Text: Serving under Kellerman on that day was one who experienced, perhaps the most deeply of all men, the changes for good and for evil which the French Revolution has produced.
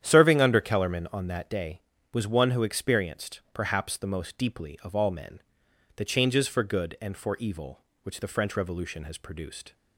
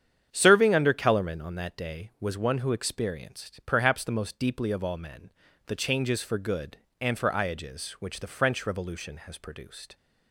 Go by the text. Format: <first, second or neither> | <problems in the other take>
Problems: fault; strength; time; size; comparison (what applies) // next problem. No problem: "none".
first | starts louder than the rest; strong; until 1.3 s; 8.5 dB; strong in the first // says "iages" for "evil"; at 7.3 s